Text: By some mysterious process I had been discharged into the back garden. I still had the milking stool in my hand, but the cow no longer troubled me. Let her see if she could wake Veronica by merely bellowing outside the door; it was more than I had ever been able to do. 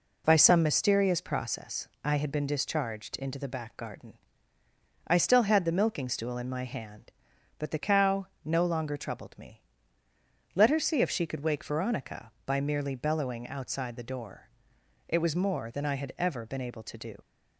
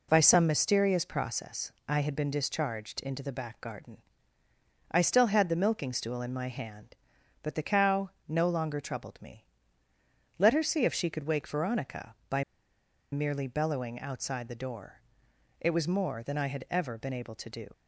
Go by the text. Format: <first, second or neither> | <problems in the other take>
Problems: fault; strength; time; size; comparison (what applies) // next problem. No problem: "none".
first | pauses between "process" and "I"; slight; at 1.7 s; 0.16 s long; slight in the first // pauses between "cow" and "no"; slight; at 8.0 s; 0.18 s long; slight in the first // pauses between "by" and "merely"; noticeable; at 12.4 s; 0.68 s long